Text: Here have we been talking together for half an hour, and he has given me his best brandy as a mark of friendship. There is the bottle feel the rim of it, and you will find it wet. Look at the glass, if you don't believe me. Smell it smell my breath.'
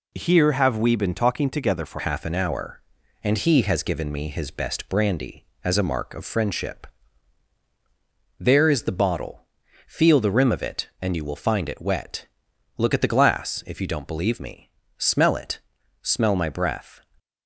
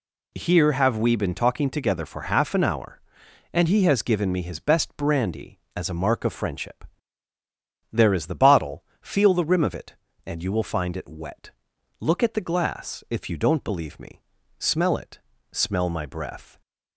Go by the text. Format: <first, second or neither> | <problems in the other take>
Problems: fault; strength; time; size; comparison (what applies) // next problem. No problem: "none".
second | changes voice at "half"; from 1.9 s on; 15.0 s long // pauses between "bottle" and "feel"; at 9.4 s; 0.42 s long; slight in the second // pauses between "it" and "smell"; at 15.6 s; 0.42 s long; slight in the second